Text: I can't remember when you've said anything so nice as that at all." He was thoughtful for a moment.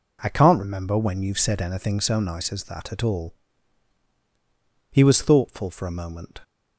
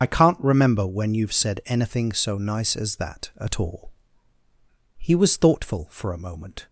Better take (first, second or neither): first